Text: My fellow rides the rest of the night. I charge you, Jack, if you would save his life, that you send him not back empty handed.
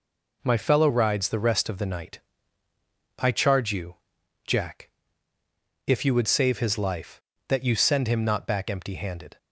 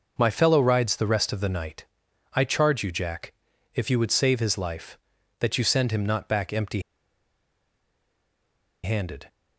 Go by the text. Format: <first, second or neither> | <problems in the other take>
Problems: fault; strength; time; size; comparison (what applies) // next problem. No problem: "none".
first | pauses between "empty" and "handed"; strong; at 6.8 s; 2.0 s long